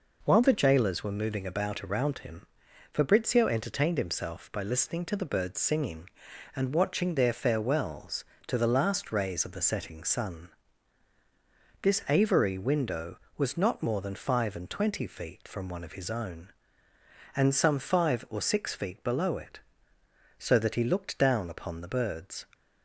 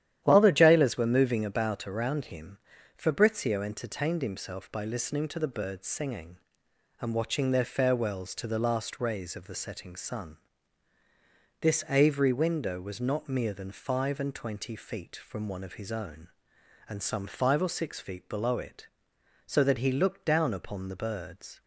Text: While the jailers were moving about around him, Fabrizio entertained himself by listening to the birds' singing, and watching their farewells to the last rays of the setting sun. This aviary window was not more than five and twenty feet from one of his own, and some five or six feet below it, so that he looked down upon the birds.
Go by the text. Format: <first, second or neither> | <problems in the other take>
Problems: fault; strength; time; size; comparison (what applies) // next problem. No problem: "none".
first | starts louder than the rest; strong; until 1.2 s; 11 dB // says "mere" for "more"; at 13.2 s